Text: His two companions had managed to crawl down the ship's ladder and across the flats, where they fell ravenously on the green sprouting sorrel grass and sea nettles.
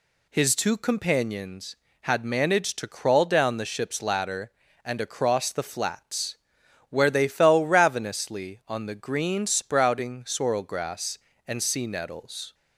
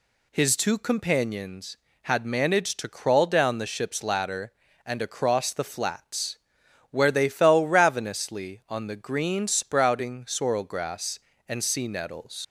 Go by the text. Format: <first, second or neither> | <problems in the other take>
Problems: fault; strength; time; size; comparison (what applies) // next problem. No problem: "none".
first | leaves "nettles" unfinished; at 12.4 s; 100 ms